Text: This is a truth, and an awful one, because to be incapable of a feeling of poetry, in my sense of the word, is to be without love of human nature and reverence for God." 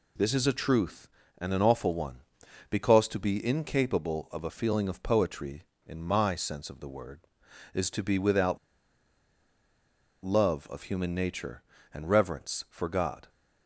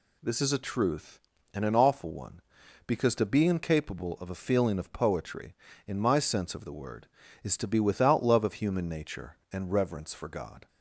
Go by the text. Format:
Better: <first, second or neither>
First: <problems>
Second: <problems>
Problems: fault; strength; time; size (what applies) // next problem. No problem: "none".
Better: second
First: pauses between "without" and "love"; strong; at 8.5 s; 1.6 s long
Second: none